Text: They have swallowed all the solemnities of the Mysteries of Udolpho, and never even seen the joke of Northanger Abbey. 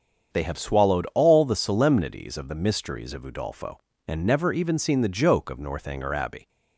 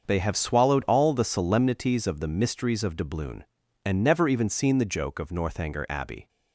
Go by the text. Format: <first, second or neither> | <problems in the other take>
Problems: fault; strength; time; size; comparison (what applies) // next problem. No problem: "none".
first | starts louder than the rest; until 1.0 s; 6.5 dB; strong in the first // says "Doubloon" for "Udolpho"; at 2.9 s